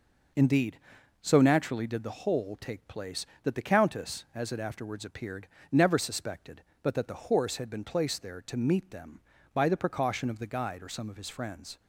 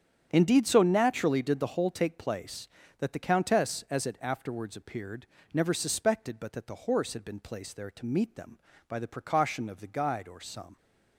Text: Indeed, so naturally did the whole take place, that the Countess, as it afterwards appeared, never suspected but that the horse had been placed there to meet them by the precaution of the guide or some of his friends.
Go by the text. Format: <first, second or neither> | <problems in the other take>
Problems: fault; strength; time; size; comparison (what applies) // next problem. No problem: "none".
first | starts louder than the rest; strong; until 1.3 s; 9 dB // stops before "of his friends"; at 10.7 s